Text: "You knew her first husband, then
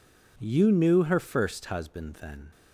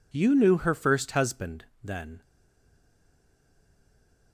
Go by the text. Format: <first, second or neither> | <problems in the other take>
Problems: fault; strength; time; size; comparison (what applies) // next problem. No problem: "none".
first | stays silent after the last word; from 2.2 s on; 2.1 s long